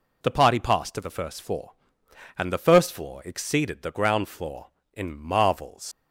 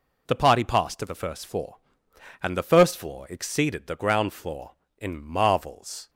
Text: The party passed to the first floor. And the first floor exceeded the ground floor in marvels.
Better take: second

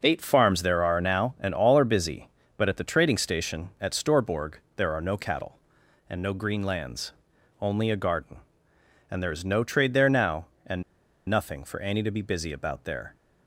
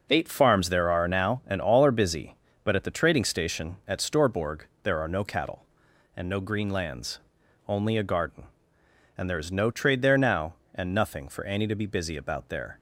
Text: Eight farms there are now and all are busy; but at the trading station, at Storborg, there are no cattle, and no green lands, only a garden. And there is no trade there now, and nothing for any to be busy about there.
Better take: second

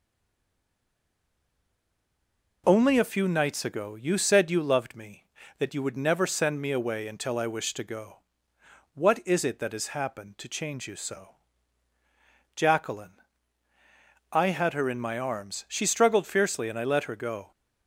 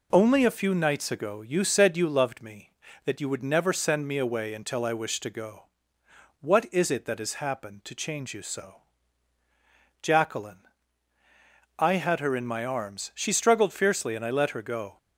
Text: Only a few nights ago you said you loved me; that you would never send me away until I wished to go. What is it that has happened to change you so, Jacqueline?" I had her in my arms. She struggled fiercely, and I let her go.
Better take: second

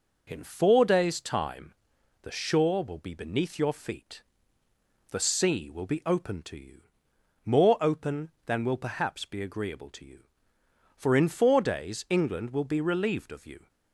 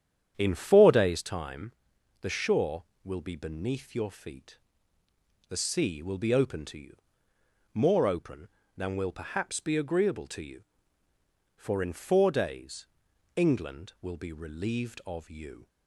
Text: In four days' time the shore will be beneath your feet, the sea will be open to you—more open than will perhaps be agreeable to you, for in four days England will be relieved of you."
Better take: first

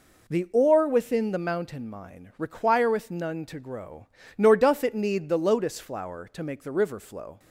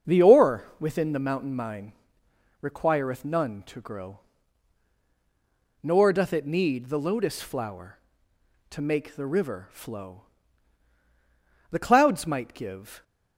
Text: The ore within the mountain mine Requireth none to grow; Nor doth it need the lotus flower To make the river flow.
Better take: first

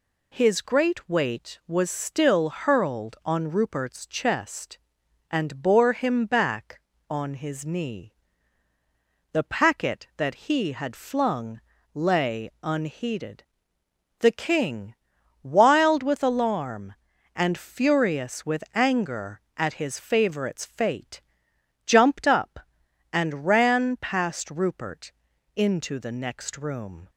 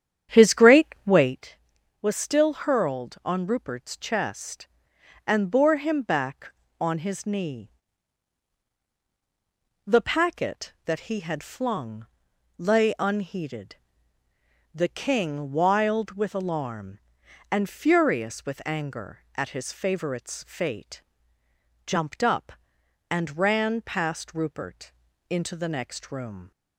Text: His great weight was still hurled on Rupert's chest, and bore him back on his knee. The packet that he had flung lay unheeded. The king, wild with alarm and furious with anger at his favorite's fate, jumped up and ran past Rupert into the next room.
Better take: first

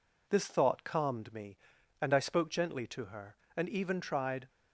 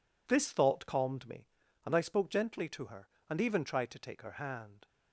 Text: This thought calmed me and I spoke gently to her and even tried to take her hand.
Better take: second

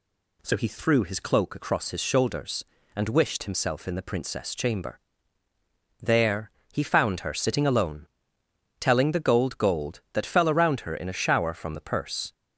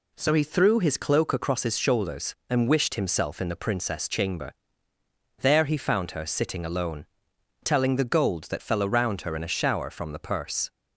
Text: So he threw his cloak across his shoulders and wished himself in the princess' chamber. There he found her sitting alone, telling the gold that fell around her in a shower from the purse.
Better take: second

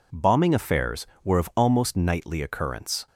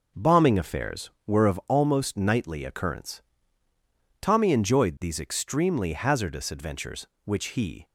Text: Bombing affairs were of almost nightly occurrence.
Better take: first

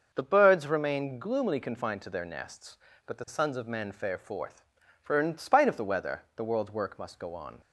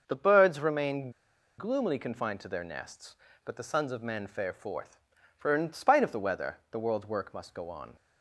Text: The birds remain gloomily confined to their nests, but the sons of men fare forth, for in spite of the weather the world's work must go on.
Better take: first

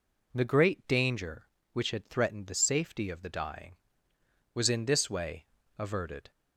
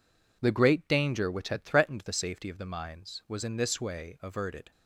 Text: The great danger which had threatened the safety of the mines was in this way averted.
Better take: second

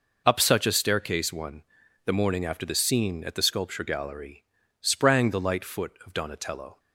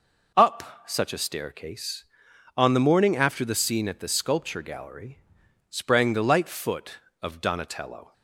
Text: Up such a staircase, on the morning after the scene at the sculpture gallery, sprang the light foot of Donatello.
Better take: second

